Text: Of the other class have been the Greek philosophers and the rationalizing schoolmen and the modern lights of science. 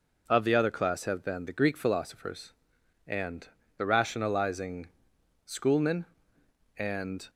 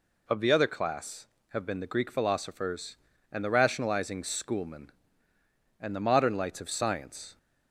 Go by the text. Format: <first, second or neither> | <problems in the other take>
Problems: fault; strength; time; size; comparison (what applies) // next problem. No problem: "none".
second | pauses between "and" and "the"; slight; at 3.4 s; 0.30 s long // pauses between "rationalizing" and "schoolmen"; noticeable; at 4.8 s; 0.58 s long // stops before "the modern lights of science"; at 7.2 s